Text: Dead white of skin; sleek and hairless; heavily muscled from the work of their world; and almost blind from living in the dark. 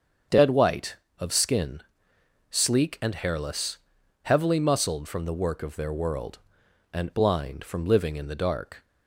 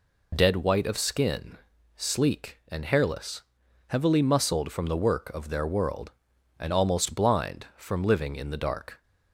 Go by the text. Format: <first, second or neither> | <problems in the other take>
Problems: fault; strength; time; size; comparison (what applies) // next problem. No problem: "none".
second | starts louder than the rest; strong; until 1.5 s; 7.5 dB // skips "almost"; at 7.1 s